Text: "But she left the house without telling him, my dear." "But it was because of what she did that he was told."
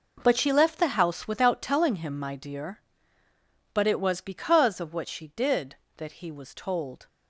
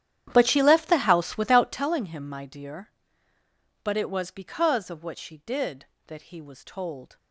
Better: first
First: none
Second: starts louder than the rest; strong; until 1.8 s; 10.5 dB

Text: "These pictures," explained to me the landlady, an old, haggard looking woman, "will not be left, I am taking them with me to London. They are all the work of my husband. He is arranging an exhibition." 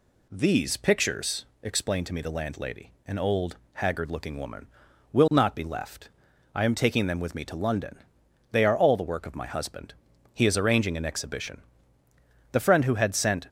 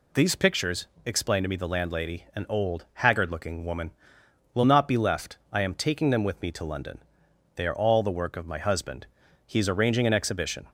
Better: second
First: goes on to say "The friend who had sent"; noticeable; from 12.5 s on; 0.96 s long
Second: none

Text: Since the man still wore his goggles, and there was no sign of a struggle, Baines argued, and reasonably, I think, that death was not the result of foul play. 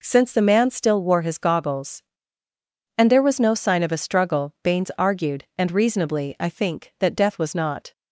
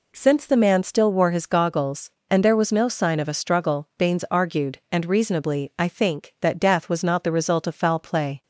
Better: second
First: stops before "the result of foul play"; at 7.9 s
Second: none

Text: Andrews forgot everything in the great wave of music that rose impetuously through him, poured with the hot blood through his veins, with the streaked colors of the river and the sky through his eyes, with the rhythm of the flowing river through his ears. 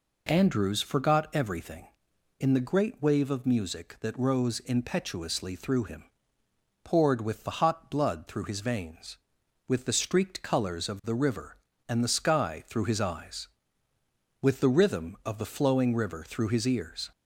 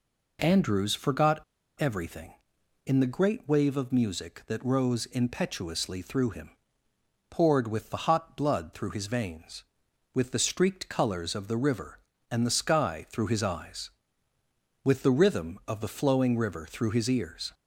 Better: first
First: none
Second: pauses between "forgot" and "everything"; slight; at 1.4 s; 0.35 s long

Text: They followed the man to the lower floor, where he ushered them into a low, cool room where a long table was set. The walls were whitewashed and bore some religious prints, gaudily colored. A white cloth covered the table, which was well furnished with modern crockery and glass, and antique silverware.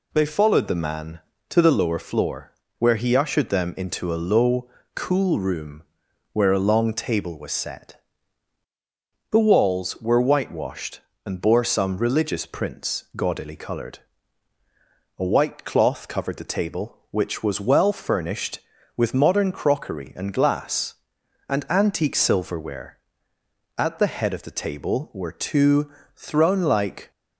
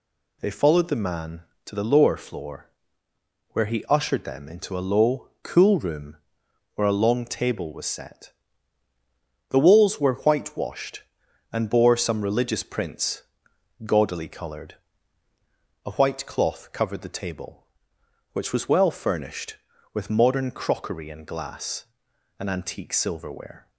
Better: second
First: pauses between "room" and "where"; noticeable; at 5.8 s; 0.50 s long // goes on to say "At the head of the table were two throne like"; strong; from 23.7 s on; 3.3 s long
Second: pauses between "room" and "where"; noticeable; at 6.1 s; 0.60 s long

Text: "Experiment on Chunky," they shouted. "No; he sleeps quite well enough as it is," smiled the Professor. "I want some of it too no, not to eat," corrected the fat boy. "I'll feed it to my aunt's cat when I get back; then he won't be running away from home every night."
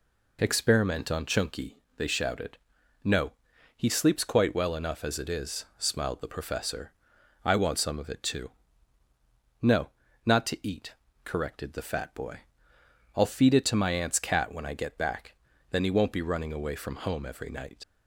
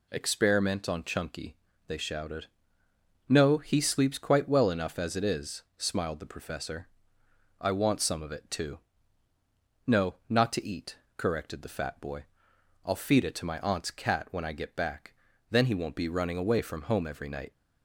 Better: second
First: pauses between "too" and "no"; at 8.4 s; 1.1 s long // leaves "night" unfinished; at 17.8 s; 60 ms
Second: pauses between "too" and "no"; at 8.7 s; 1.0 s long

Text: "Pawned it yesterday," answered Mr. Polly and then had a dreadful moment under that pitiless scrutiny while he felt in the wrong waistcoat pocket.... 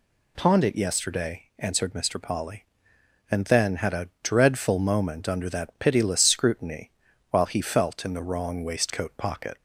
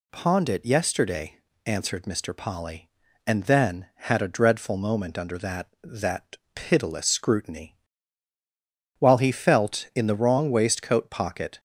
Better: first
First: pauses between "scrutiny" and "while"; at 6.9 s; 0.38 s long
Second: says "that" twice; at 5.8 s // pauses between "scrutiny" and "while"; at 7.7 s; 1.2 s long

